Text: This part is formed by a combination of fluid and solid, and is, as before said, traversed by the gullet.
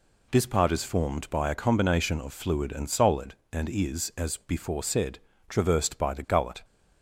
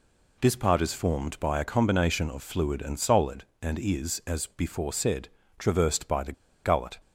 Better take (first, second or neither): first